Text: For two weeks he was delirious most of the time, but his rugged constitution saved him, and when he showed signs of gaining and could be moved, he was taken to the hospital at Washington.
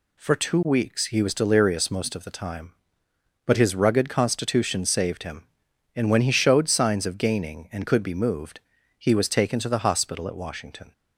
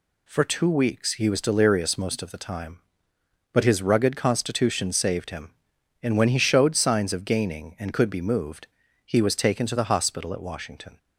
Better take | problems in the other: neither | none

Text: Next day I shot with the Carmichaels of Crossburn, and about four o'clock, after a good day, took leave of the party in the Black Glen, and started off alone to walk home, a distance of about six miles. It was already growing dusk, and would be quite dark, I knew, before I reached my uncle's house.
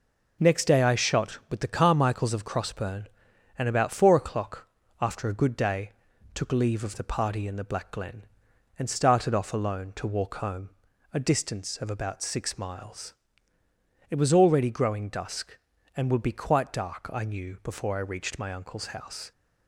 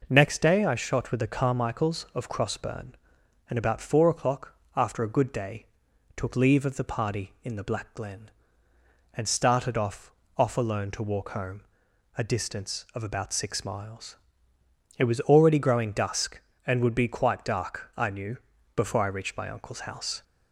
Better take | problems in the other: first | says "off" twice; at 10.3 s

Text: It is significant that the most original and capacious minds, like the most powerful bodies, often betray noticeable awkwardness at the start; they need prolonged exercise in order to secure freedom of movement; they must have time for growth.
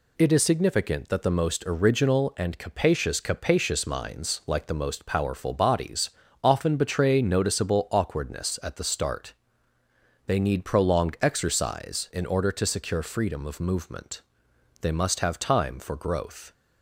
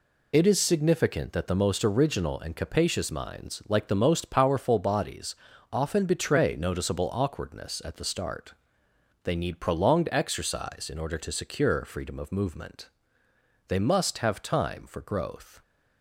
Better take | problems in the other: second | says "capacious" twice; at 3.1 s

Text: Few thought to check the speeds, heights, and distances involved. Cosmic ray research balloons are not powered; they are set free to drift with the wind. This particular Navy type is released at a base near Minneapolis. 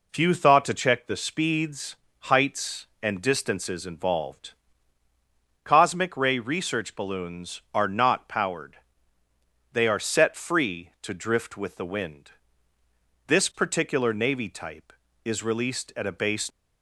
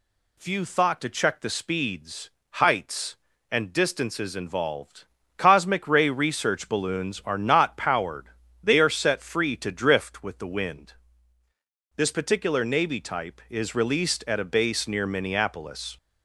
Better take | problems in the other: second | stops before "near Minneapolis"; at 16.5 s

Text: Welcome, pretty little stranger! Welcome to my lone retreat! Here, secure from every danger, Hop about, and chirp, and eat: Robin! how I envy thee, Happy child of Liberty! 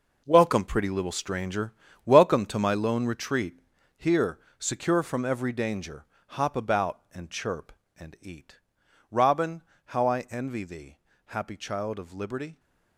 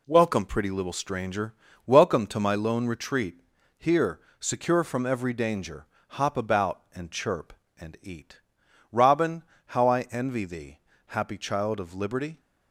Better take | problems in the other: second | gets quieter; strong; throughout; 12 dB

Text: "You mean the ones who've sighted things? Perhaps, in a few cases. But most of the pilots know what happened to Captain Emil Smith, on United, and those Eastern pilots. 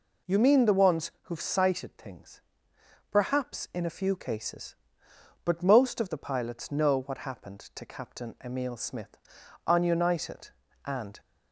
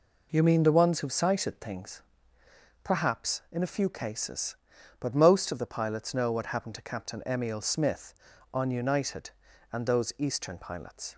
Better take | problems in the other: second | stops before "those Eastern pilots"; at 11.1 s

